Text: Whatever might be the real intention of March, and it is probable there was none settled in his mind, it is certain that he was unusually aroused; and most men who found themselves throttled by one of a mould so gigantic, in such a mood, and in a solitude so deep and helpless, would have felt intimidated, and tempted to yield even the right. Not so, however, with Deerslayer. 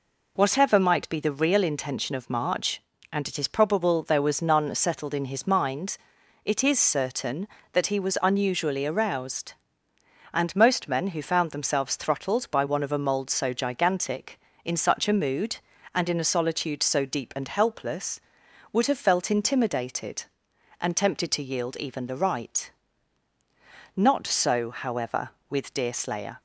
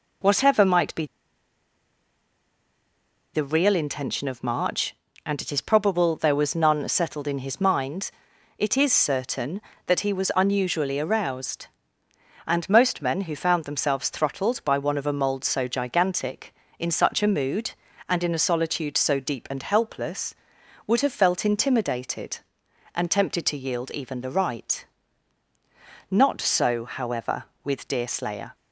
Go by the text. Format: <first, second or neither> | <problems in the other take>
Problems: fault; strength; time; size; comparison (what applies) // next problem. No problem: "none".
first | pauses between "be" and "the"; strong; at 1.0 s; 2.2 s long